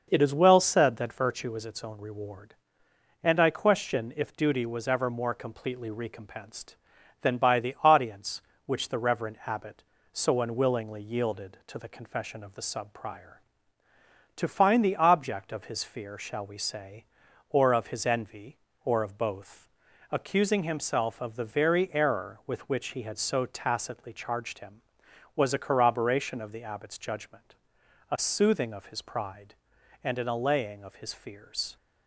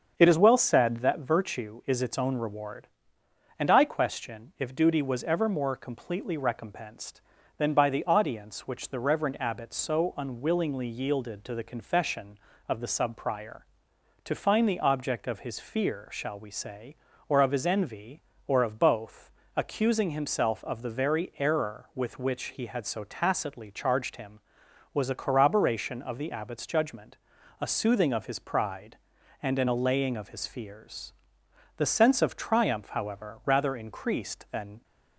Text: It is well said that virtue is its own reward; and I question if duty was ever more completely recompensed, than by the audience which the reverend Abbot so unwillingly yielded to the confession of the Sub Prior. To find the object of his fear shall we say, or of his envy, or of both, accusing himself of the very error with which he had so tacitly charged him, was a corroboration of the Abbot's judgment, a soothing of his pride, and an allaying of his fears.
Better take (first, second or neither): first